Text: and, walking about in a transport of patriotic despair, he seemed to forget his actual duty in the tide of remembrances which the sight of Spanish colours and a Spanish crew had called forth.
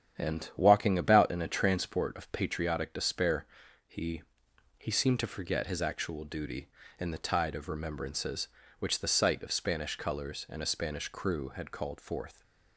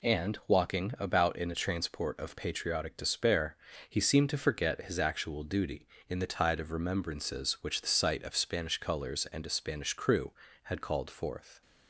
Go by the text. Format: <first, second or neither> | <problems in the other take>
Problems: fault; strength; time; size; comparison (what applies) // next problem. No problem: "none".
second | starts louder than the rest; strong; until 1.2 s; 9 dB // says "he" twice; at 4.7 s